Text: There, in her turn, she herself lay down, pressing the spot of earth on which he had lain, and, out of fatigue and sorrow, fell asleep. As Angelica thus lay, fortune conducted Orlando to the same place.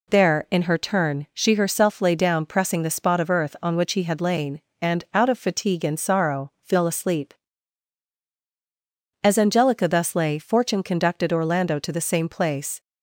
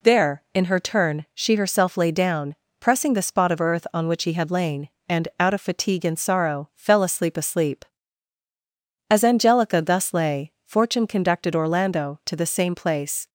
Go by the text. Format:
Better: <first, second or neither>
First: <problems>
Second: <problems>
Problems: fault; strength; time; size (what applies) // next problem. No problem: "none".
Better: first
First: none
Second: says "asleep" twice; at 7.3 s